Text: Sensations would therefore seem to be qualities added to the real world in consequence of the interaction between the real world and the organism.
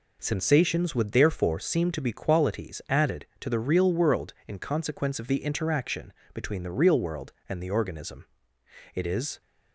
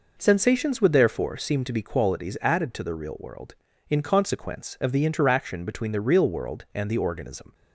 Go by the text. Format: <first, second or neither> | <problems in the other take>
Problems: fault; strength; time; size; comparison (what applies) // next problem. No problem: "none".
second | pauses between "interaction" and "between"; slight; at 6.1 s; 0.22 s long // goes on to say "It is"; slight; from 8.9 s on; 0.48 s long